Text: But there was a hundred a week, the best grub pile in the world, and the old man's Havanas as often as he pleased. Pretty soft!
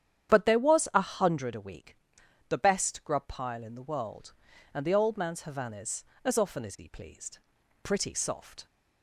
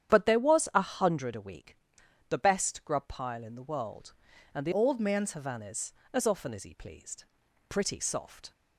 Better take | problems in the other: first | starts louder than the rest; strong; until 1.1 s; 9.5 dB; strong in the first // changes voice from "old" to "man's"; from 4.7 to 5.3 s; 0.6 s long

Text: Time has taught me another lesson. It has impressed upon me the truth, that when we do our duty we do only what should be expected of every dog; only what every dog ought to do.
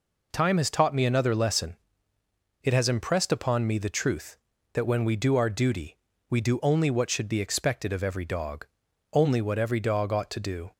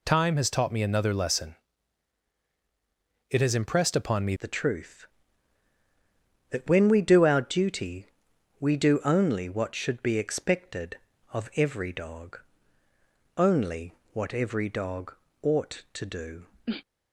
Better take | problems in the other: first | changes voice at "the"; from 4.3 s on; 12.1 s long // pauses between "duty" and "we"; noticeable; at 8.0 s; 0.54 s long; slight in the first // pauses between "only" and "what"; slight; at 13.9 s; 0.18 s long // pauses between "dog" and "ought"; slight; at 15.1 s; 0.30 s long

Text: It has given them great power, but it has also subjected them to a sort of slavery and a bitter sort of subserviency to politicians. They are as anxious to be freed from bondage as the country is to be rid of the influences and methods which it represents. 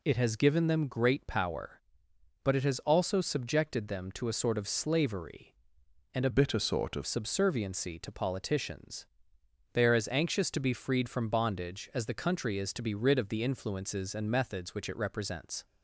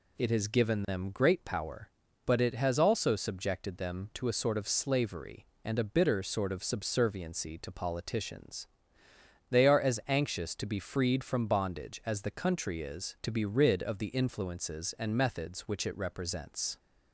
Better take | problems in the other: second | changes voice from "bitter" to "of"; from 6.3 to 7.0 s; 0.7 s long

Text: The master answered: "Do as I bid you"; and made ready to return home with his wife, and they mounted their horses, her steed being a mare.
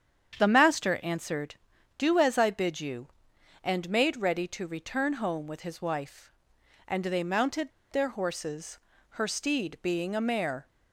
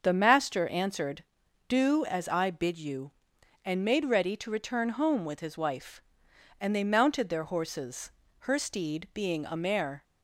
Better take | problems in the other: second | starts louder than the rest; strong; until 1.4 s; 8 dB; also in the second // pauses between "mounted" and "their"; slight; at 7.7 s; 0.20 s long

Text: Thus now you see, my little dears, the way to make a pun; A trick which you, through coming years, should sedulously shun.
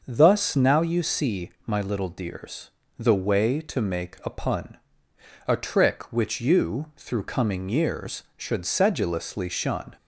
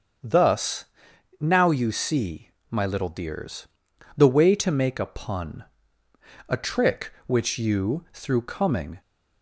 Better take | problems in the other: first | starts louder than the rest; strong; until 1.7 s; 7 dB; also in the first // pauses between "Thus" and "now"; noticeable; at 0.8 s; 0.54 s long // stops before "years should sedulously shun"; at 9.0 s

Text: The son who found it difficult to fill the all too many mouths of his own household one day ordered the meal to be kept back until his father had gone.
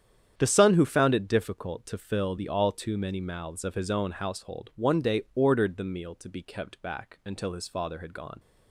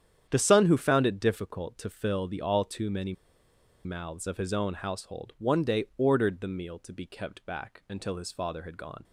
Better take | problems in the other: first | starts louder than the rest; strong; until 1.3 s; 9 dB; strong in the first // pauses between "many" and "mouths"; noticeable; at 3.1 s; 0.71 s long

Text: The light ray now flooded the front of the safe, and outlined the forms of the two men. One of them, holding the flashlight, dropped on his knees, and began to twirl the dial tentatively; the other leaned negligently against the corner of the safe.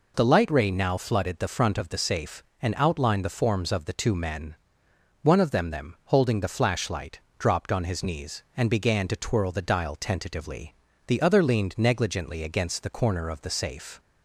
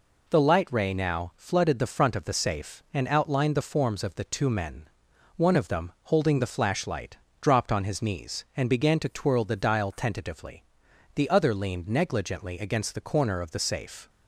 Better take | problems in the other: second | says "them" twice; at 5.7 s

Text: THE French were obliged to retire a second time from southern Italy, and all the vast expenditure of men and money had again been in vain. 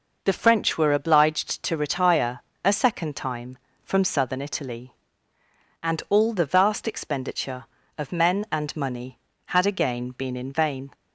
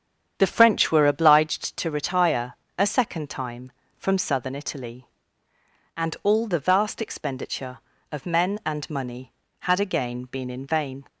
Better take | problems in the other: first | starts louder than the rest; strong; until 1.5 s; 8.5 dB // pauses between "retire" and "a"; slight; at 2.5 s; 0.22 s long; slight in the first

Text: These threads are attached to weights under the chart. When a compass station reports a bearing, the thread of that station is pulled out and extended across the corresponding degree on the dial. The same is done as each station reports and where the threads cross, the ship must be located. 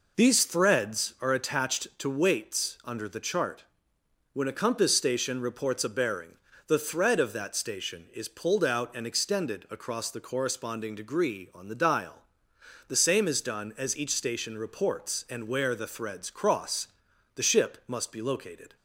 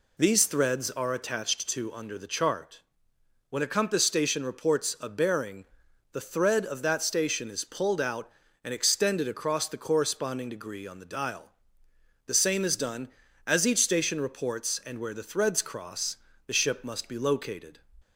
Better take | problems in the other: first | skips "weights"; at 1.9 s

